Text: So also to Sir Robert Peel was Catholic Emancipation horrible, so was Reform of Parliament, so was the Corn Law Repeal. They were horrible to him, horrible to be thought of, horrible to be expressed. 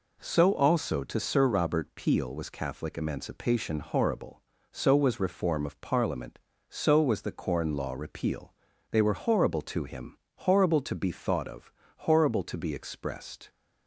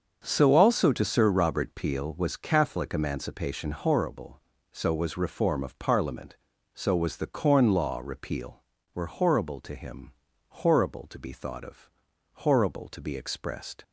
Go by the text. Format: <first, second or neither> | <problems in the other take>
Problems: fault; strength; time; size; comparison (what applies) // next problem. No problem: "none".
first | starts louder than the rest; until 1.2 s; 6.5 dB // skips "They"; at 8.7 s